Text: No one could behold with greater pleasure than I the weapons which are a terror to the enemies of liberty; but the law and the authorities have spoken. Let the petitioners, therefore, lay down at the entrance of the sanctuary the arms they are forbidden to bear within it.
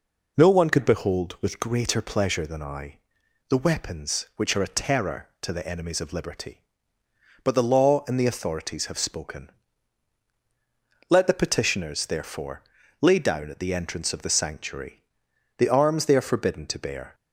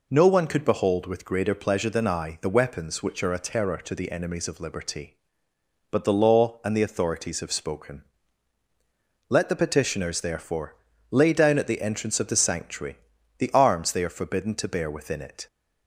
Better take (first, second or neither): second